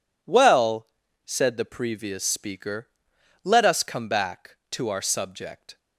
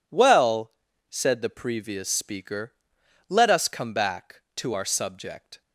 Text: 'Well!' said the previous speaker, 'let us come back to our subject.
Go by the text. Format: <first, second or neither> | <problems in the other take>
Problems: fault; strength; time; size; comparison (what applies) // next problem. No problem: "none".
neither | none